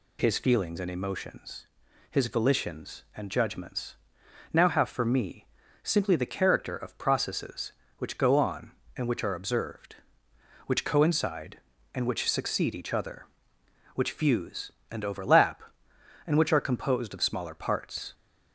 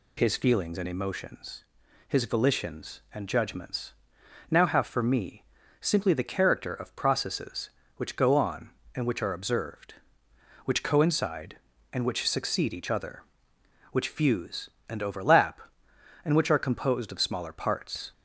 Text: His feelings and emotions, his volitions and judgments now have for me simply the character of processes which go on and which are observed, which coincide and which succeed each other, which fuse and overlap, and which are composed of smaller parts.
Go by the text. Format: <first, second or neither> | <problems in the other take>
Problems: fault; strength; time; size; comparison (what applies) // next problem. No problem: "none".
neither | pauses between "judgments" and "now"; noticeable; the same in both // pauses between "me" and "simply"; slight; the same in both